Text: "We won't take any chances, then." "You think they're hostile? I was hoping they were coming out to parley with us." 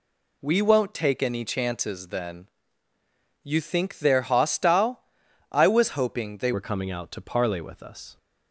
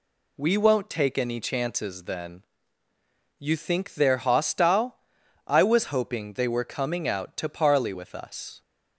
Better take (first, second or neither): second